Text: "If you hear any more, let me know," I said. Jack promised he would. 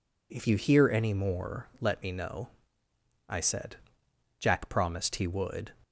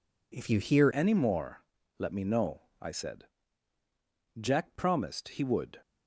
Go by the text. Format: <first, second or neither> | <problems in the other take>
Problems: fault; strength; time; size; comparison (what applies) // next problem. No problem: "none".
first | changes voice at "any"; from 0.9 s on; 4.8 s long